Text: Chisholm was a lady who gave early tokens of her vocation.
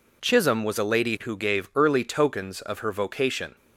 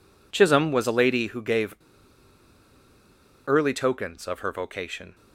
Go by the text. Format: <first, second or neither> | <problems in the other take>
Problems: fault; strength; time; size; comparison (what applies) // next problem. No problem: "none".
first | pauses between "gave" and "early"; strong; at 1.7 s; 1.7 s long